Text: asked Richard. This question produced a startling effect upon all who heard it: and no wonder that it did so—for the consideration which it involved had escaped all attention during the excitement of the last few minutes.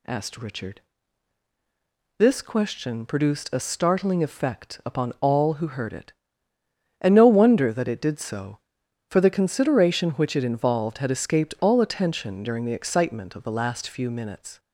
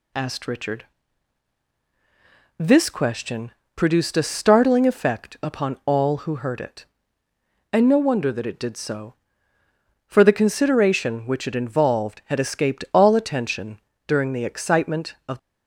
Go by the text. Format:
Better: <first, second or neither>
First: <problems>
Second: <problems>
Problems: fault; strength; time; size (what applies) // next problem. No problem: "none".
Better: first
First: none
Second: pauses between "question" and "produced"; slight; at 3.5 s; 0.24 s long // pauses between "attention" and "during"; slight; at 13.7 s; 0.28 s long // stops before "the last few minutes"; at 15.3 s